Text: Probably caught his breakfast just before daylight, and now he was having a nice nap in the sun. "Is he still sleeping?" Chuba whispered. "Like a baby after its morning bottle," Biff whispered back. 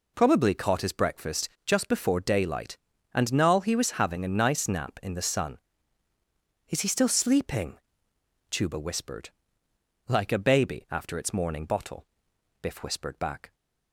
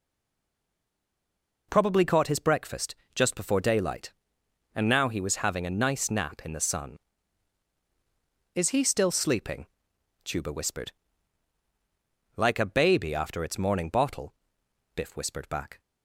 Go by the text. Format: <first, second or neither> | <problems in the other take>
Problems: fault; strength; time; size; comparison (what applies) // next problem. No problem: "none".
first | stays silent before the first word; noticeable; until 1.6 s; 1.6 s long // pauses between "breakfast" and "just"; slight; at 2.9 s; 0.18 s long; slight in the first